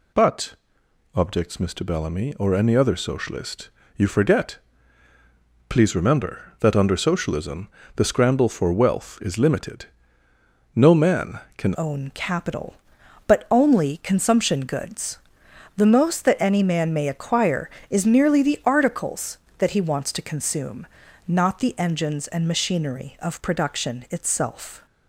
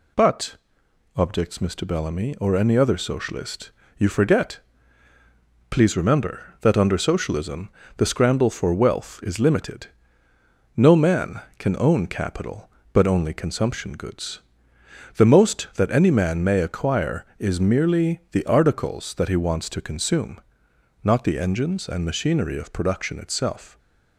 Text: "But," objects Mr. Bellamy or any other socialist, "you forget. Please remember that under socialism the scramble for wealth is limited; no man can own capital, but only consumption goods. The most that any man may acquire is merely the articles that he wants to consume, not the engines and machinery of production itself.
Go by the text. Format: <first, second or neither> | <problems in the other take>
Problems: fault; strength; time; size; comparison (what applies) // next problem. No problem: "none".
second | pauses between "socialism" and "the"; slight; at 7.6 s; 0.28 s long; slight in the second // changes voice at "own"; from 11.7 s on; 13.1 s long